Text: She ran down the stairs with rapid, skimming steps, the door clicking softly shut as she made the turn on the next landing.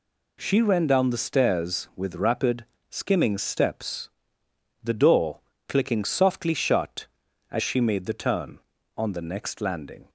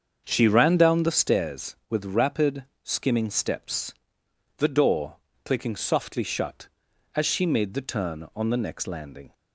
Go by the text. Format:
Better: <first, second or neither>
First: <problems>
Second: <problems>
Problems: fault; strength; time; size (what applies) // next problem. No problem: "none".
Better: first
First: pauses between "door" and "clicking"; slight; at 5.4 s; 0.26 s long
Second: starts louder than the rest; until 1.4 s; 7 dB // pauses between "door" and "clicking"; slight; at 5.1 s; 0.28 s long